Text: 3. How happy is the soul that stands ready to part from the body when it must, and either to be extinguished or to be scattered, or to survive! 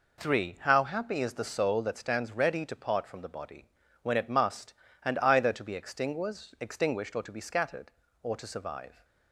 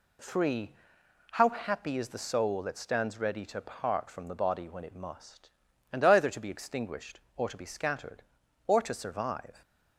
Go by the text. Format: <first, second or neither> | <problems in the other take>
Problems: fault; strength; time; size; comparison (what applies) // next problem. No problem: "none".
second | pauses between "body" and "when"; slight; at 3.6 s; 0.34 s long // says "extinguished" twice; at 6.5 s